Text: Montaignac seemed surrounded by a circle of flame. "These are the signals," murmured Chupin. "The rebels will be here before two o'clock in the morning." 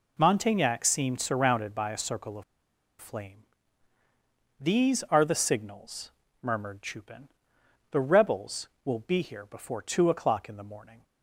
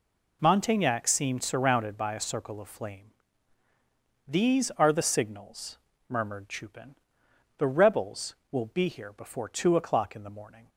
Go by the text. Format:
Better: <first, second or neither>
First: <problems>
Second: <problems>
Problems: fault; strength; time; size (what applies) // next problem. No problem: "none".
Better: second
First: pauses between "of" and "flame"; noticeable; at 2.4 s; 0.57 s long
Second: none